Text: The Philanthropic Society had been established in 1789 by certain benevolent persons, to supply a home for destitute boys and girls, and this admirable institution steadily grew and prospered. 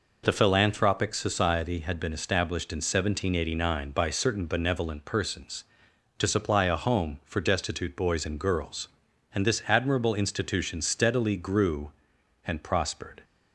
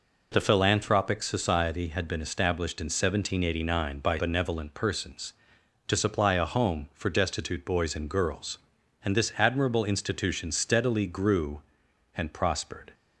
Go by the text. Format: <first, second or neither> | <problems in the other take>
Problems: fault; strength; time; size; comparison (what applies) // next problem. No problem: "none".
first | skips "certain"; at 4.1 s